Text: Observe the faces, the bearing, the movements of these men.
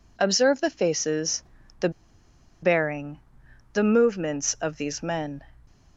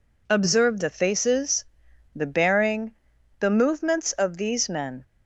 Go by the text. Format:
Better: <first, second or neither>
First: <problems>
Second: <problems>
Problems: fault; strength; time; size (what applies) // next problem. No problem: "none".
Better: second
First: pauses between "the" and "bearing"; noticeable; at 1.8 s; 0.72 s long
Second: none